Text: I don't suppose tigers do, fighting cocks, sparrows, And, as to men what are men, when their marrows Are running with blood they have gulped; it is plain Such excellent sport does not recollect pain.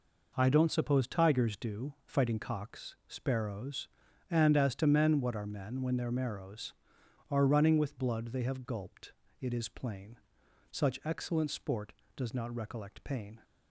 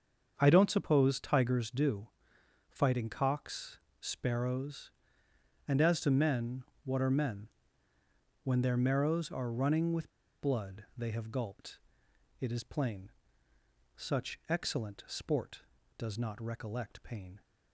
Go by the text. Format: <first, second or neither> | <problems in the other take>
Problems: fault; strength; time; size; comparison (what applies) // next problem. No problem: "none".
first | starts louder than the rest; until 1.3 s; 6.5 dB // pauses between "men" and "what"; slight; at 6.6 s; 0.18 s long // pauses between "with" and "blood"; slight; at 10.1 s; 0.29 s long // pauses between "plain" and "Such"; noticeable; at 13.1 s; 0.86 s long; noticeable in the first